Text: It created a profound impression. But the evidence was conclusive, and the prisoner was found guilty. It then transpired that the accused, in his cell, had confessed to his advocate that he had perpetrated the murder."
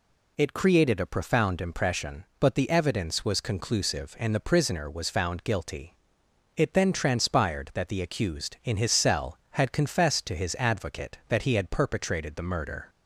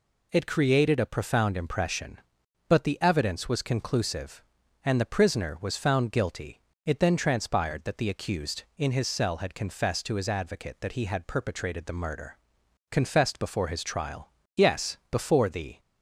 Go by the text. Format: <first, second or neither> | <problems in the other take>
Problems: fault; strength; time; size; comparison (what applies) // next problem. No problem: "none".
first | goes on to say "Confessed before his trial Yes before the"; strong; from 12.9 s on; 2.8 s long